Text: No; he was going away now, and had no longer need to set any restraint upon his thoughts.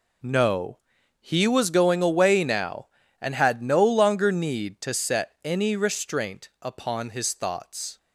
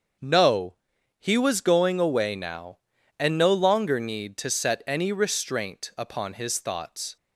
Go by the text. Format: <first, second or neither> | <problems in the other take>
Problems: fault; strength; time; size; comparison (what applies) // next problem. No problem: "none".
first | starts louder than the rest; until 1.6 s; 6.5 dB // skips "had"; at 3.3 s